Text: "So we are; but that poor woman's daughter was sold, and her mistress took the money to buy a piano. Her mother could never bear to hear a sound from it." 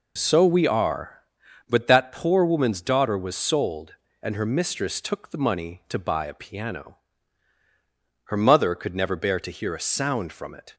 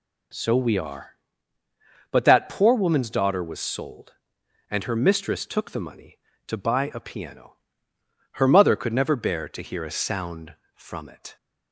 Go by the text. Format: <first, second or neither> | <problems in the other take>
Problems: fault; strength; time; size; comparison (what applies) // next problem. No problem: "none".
neither | none